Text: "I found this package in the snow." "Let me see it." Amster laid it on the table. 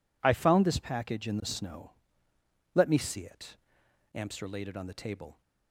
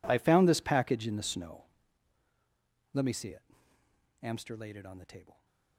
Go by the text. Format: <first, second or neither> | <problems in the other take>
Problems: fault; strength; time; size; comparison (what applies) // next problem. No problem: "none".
first | gets quieter; strong; throughout; 22 dB